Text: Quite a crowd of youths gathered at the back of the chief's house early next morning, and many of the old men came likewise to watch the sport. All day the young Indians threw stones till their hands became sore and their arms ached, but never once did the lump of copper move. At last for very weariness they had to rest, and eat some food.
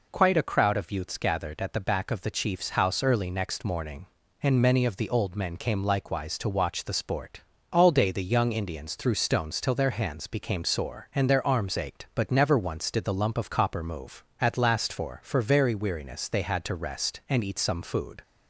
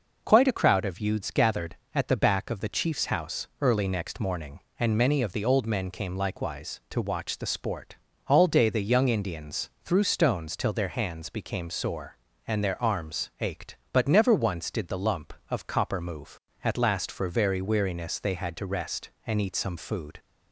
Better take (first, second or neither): second